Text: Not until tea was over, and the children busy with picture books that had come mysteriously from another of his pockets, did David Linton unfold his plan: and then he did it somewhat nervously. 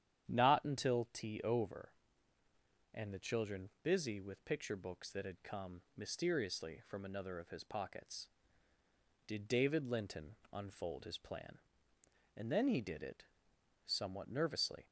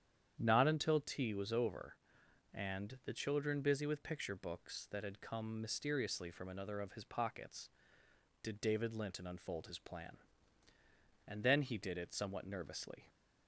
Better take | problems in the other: second | starts louder than the rest; strong; until 1.3 s; 9.5 dB; strong in the second // skips "was"; at 1.4 s // pauses between "Linton" and "unfold"; slight; at 10.3 s; 0.16 s long // pauses between "it" and "somewhat"; noticeable; at 13.2 s; 0.60 s long

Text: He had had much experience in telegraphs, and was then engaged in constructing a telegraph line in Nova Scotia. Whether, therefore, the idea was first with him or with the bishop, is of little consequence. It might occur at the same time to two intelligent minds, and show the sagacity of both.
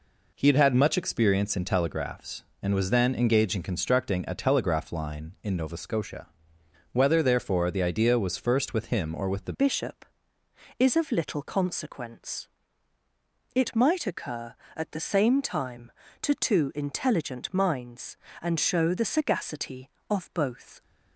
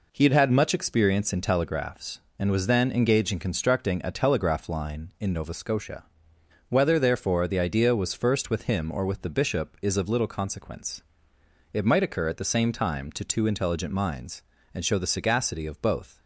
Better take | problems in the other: second | changes voice at "bishop"; from 9.5 s on; 11.3 s long

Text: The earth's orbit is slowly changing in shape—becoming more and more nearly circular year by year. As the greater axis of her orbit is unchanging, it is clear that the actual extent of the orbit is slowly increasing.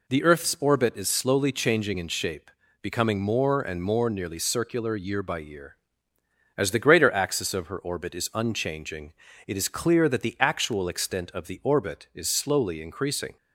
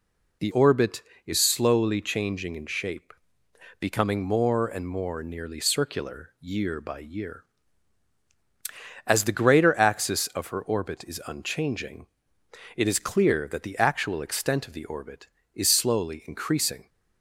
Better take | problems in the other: first | skips "earth's"; at 0.5 s

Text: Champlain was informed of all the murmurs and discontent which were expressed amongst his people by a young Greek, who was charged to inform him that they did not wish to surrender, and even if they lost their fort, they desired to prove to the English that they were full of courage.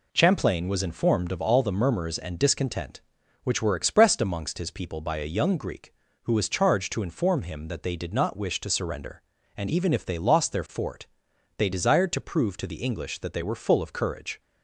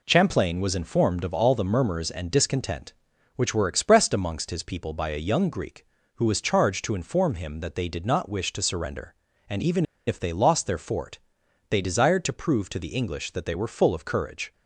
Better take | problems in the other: first | pauses between "even" and "if"; slight; at 9.8 s; 0.22 s long

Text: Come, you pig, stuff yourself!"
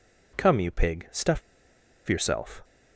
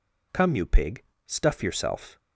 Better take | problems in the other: second | pauses between "stuff" and "yourself"; noticeable; at 1.4 s; 0.69 s long

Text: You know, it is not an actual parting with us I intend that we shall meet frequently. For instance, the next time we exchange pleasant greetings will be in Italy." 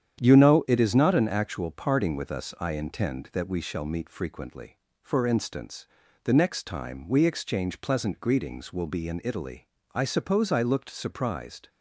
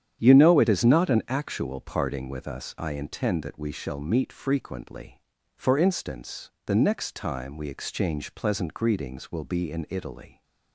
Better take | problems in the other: second | starts louder than the rest; strong; until 1.2 s; 9 dB; strong in the second // goes on to say "I suppose I looked surprised"; strong; from 9.9 s on; 1.7 s long

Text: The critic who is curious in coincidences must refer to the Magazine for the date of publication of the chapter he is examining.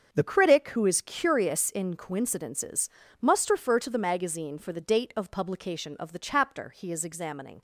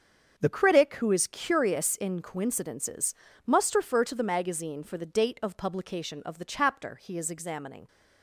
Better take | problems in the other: neither | starts louder than the rest; the same in both // pauses between "coincidences" and "must"; slight; the same in both

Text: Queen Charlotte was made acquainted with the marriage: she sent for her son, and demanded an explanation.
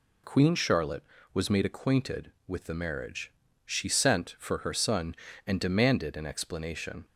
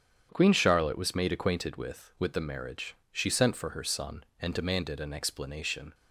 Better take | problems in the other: first | starts louder than the rest; strong; until 1.3 s; 8.5 dB // says "with" twice; at 2.1 s

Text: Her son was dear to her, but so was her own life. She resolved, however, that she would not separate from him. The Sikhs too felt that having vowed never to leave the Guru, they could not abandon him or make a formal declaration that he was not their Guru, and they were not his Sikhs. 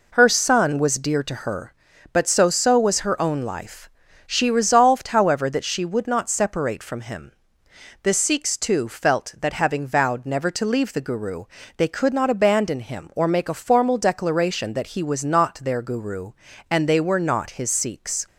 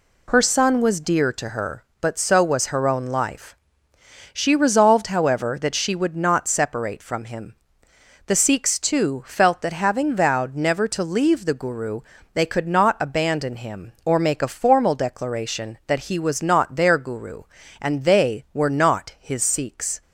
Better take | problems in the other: second | says "so" twice; at 2.5 s

